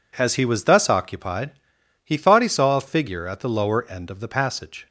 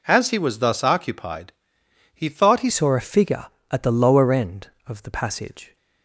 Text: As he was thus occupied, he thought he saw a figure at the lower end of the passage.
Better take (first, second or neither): first